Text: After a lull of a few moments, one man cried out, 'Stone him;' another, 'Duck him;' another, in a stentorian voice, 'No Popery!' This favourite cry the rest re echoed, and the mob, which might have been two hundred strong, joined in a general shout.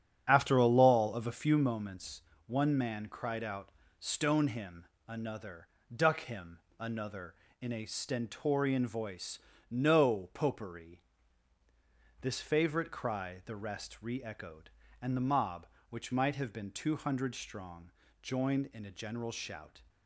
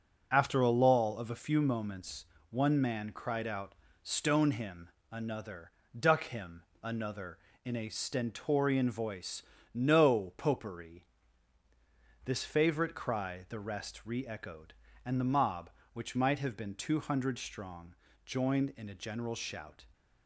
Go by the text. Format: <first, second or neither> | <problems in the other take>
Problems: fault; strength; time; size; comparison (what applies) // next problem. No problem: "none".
second | starts louder than the rest; strong; until 1.8 s; 8.5 dB